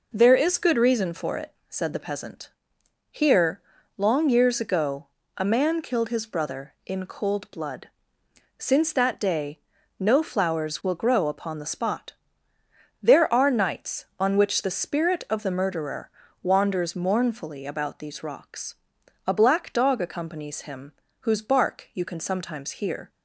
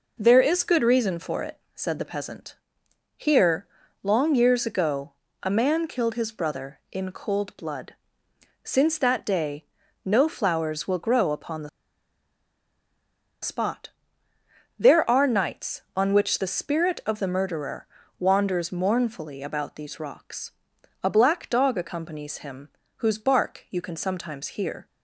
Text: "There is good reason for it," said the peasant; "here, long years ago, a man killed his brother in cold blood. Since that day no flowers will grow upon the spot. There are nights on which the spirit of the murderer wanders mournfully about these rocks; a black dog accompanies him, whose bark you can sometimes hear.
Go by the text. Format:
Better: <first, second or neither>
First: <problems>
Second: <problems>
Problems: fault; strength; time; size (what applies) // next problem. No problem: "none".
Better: first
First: pauses between "day" and "no"; at 9.5 s; 0.38 s long // pauses between "murderer" and "wanders"; slight; at 16.1 s; 0.32 s long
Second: pauses between "day" and "no"; at 9.6 s; 0.38 s long // pauses between "the" and "spot"; strong; at 11.6 s; 1.7 s long // pauses between "murderer" and "wanders"; slight; at 17.8 s; 0.32 s long